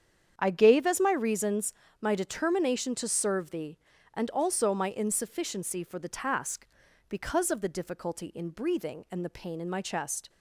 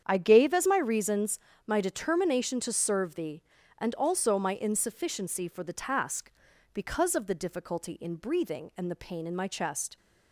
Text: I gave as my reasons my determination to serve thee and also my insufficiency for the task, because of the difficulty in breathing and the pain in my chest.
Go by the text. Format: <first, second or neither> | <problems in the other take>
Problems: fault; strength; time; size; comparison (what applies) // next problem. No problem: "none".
neither | starts louder than the rest; strong; the same in both // pauses between "reasons" and "my"; slight; the same in both